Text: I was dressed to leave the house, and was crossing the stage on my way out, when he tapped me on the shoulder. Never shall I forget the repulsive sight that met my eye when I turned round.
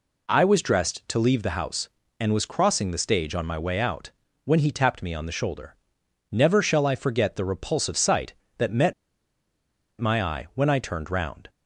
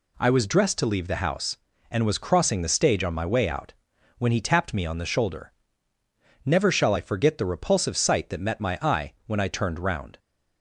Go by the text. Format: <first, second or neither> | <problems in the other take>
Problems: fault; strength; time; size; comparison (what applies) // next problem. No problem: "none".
second | pauses between "met" and "my"; at 8.9 s; 1.0 s long